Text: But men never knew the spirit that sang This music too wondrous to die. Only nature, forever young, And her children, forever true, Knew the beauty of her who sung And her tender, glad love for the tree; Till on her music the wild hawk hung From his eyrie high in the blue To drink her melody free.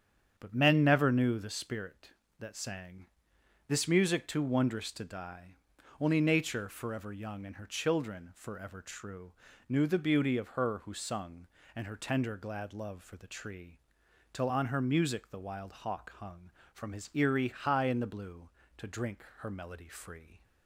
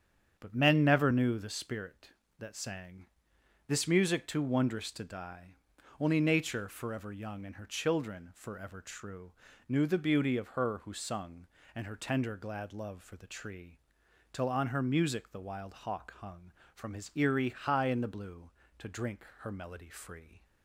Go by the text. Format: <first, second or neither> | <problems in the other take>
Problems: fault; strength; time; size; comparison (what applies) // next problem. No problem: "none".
neither | starts louder than the rest; strong; the same in both // pauses between "sang" and "This"; noticeable; the same in both // pauses between "drink" and "her"; slight; the same in both